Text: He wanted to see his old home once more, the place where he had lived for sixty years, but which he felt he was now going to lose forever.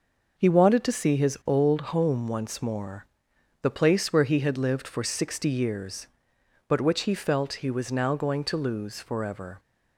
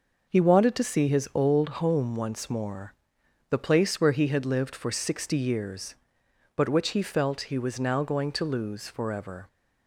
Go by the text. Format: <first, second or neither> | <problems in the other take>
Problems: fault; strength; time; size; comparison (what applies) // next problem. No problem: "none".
neither | none